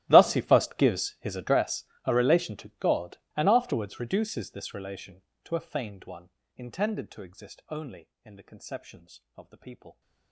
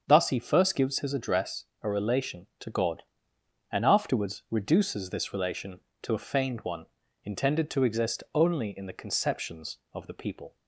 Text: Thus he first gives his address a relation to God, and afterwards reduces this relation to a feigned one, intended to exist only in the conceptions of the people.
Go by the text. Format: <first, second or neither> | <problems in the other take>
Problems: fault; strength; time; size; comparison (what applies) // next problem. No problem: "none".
second | gets quieter; strong; throughout; 25 dB // starts louder than the rest; strong; until 1.0 s; 15.5 dB; strong in the second // pauses between "address" and "a"; slight; at 1.8 s; 0.20 s long; slight in the second